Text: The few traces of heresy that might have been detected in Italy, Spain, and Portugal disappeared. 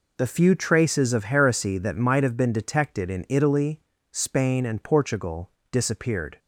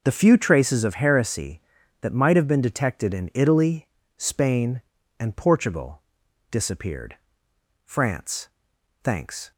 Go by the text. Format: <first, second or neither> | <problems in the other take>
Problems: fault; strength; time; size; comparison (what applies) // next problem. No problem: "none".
first | pauses between "Portugal" and "disappeared"; noticeable; at 6.0 s; 0.50 s long; slight in the first // goes on to say "France thanks"; from 7.8 s on; 1.6 s long